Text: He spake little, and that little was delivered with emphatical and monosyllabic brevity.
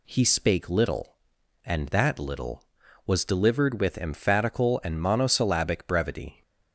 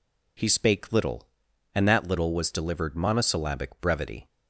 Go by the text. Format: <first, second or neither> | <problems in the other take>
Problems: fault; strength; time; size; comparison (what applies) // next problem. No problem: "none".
first | skips "with emphatical and"; at 2.9 s